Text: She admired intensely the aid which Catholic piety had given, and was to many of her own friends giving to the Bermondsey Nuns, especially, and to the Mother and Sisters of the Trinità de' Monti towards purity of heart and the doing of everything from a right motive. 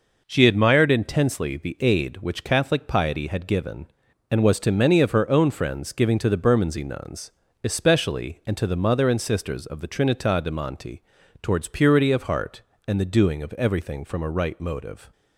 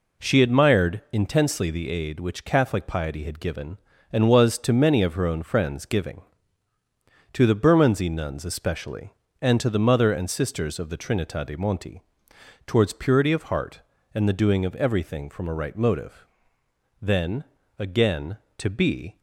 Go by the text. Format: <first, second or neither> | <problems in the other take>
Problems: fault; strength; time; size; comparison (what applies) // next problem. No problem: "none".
first | pauses between "Monti" and "towards"; noticeable; at 12.0 s; 0.64 s long; also in the first // goes on to say "Then again to be"; strong; from 17.0 s on; 2.1 s long